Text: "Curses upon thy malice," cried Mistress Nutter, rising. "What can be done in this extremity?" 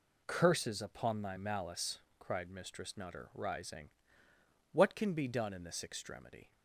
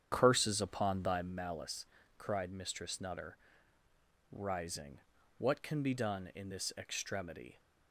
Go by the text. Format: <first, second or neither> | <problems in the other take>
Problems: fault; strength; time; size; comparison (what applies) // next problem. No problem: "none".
first | starts louder than the rest; strong; until 1.3 s; 8 dB